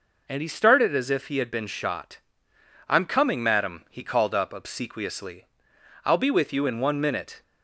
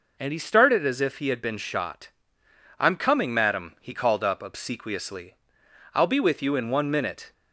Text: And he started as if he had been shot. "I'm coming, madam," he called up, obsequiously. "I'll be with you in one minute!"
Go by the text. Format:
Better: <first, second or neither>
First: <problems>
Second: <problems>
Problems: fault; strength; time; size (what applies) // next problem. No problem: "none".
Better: neither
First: none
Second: none